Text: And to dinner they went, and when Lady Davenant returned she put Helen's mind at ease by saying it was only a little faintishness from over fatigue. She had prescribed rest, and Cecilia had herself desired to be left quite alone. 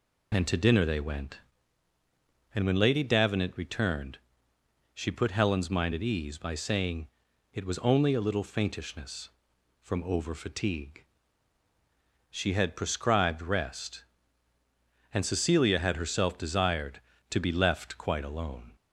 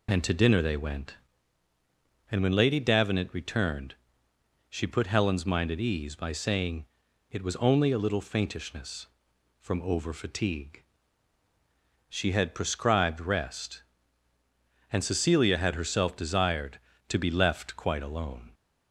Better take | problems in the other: neither | pauses between "returned" and "she"; noticeable; the same in both // pauses between "saying" and "it"; the same in both

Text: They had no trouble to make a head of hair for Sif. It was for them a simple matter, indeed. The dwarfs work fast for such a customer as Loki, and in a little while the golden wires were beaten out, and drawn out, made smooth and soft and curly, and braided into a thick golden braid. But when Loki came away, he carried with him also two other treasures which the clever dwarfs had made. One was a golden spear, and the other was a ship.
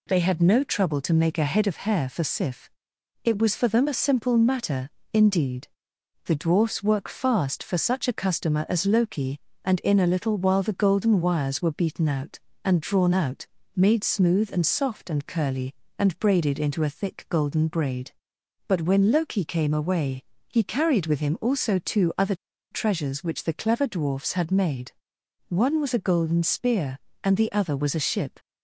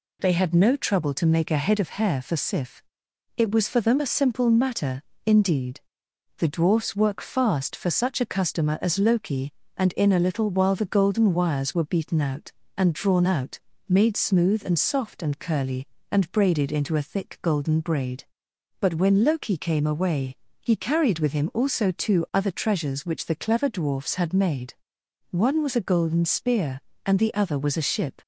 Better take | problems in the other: second | pauses between "other" and "treasures"; slight; at 22.3 s; 0.35 s long

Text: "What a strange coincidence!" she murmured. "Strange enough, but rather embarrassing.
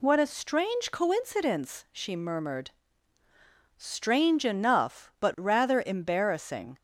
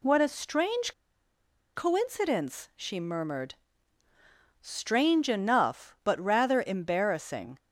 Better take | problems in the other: first | pauses between "strange" and "coincidence"; noticeable; at 0.9 s; 0.85 s long

